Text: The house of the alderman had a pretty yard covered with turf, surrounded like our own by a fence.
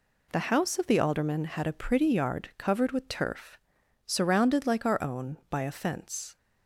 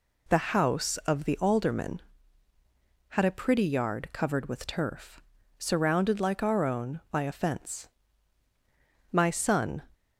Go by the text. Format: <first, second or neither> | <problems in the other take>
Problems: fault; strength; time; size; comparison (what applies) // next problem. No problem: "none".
first | goes on to say "My son"; noticeable; from 9.0 s on; 0.74 s long